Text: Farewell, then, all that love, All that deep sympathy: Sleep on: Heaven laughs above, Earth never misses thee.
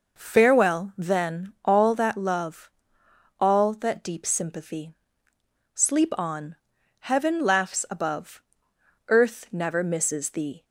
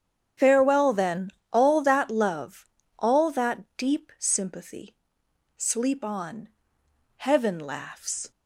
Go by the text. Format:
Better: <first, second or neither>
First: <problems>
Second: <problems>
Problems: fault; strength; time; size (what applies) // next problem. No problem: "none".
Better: first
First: none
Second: starts louder than the rest; strong; until 1.5 s; 8 dB // stops before "above Earth never misses thee"; at 8.3 s